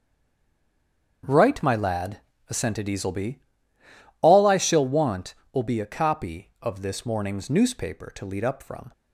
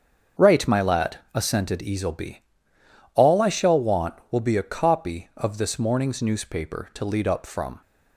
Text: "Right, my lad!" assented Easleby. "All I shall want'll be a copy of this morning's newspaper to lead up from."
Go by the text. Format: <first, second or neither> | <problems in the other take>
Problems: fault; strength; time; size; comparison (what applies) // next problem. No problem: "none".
second | stays silent before the first word; noticeable; until 1.2 s; 1.2 s long // starts louder than the rest; strong; until 2.5 s; 7.5 dB; also in the second